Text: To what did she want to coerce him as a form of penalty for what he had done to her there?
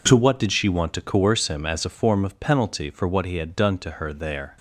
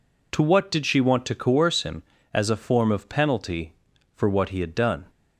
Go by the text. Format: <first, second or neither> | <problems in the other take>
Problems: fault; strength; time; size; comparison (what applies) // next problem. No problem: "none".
first | stops before "to her there"; at 5.0 s